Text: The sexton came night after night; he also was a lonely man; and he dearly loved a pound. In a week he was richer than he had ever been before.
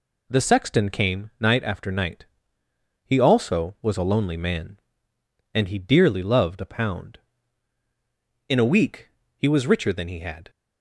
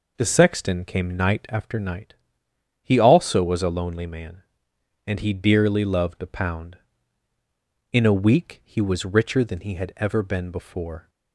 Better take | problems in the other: second | pauses between "week" and "he"; slight; at 9.0 s; 0.30 s long // stops before "ever been before"; at 10.4 s

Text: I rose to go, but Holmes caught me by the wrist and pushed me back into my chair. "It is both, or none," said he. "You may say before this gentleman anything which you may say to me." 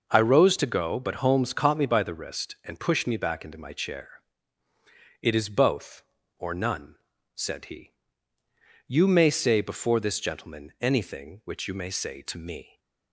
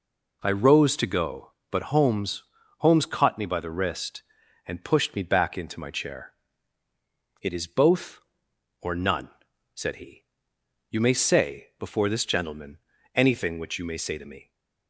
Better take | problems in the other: first | says "Holmes" twice; at 2.7 s // pauses between "gentleman" and "anything"; slight; at 12.7 s; 0.36 s long

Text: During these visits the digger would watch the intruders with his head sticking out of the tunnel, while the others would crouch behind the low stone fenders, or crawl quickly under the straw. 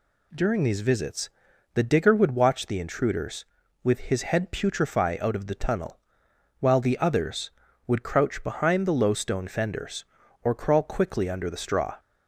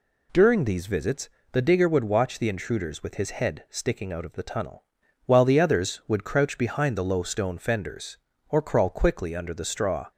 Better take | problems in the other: second | pauses between "visits" and "the"; noticeable; at 1.2 s; 0.46 s long; slight in the second // says "putrefy" for "sticking"; at 4.5 s

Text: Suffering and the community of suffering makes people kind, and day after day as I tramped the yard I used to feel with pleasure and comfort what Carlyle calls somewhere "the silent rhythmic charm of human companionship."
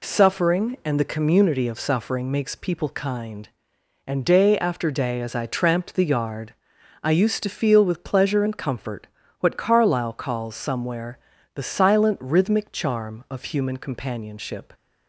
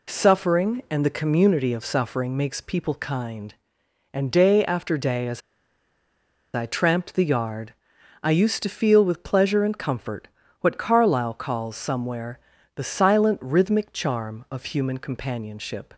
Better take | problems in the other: first | pauses between "as" and "I"; at 5.4 s; 1.1 s long // pauses between "yard" and "I"; noticeable; at 7.7 s; 0.50 s long; noticeable in the first // pauses between "comfort" and "what"; slight; at 10.2 s; 0.36 s long; slight in the first // pauses between "somewhere" and "the"; slight; at 12.3 s; 0.34 s long; slight in the first

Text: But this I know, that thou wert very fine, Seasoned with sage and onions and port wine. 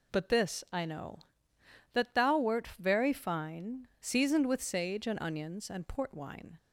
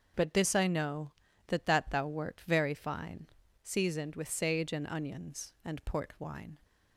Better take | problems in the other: first | starts louder than the rest; until 1.5 s; 6.5 dB // says "that" twice; at 1.6 s

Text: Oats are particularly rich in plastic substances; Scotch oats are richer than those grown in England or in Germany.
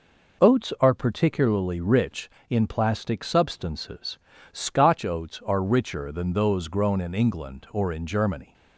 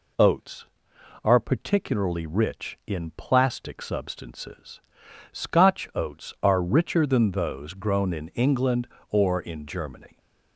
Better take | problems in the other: neither | none

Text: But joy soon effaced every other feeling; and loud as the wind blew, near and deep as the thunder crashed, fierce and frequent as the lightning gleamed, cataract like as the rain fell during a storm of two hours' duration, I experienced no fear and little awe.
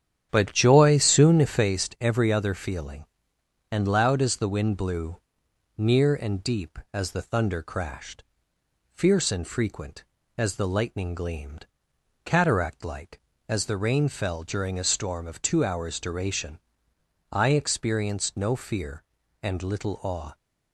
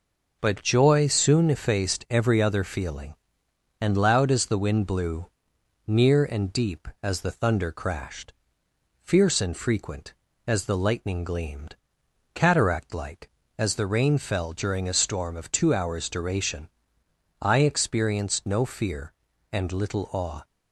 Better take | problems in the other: second | starts louder than the rest; strong; until 1.8 s; 9.5 dB

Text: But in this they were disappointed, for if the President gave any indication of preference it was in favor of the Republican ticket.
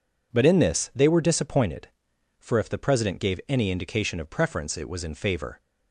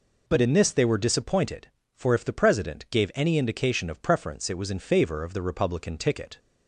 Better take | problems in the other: second | stops before "of the Republican ticket"; at 5.5 s

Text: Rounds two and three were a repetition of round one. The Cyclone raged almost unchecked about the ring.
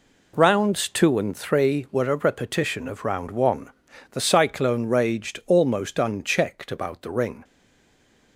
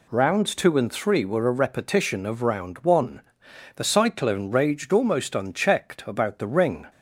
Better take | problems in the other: second | stays silent after the last word; slight; from 7.4 s on; 0.9 s long

